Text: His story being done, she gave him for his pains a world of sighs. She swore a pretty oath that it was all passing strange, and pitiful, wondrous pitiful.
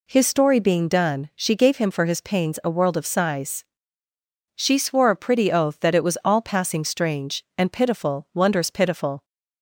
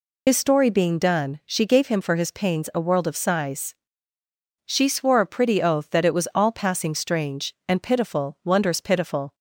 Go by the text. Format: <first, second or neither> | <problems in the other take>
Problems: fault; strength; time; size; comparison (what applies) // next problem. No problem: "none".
first | loses the start of "His"; at 0.2 s; 80 ms